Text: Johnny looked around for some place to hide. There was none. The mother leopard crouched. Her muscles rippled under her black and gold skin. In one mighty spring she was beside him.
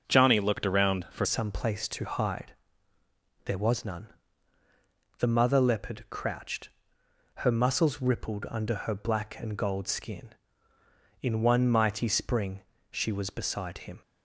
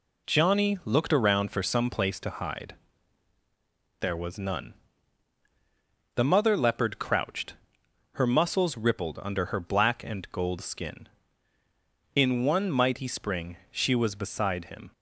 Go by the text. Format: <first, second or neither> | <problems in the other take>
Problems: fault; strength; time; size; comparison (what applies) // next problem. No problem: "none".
second | starts louder than the rest; until 1.0 s; 6.5 dB // changes voice at "some"; from 1.2 s on; 12.8 s long // pauses between "spring" and "she"; slight; at 12.6 s; 0.30 s long